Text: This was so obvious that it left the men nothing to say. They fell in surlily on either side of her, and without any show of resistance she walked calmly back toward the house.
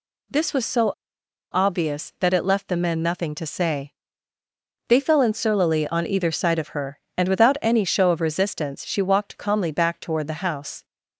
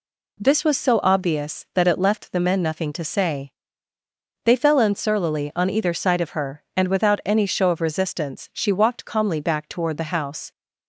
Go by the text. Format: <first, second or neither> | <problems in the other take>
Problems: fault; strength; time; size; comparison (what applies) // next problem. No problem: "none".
second | pauses between "so" and "obvious"; noticeable; at 0.9 s; 0.59 s long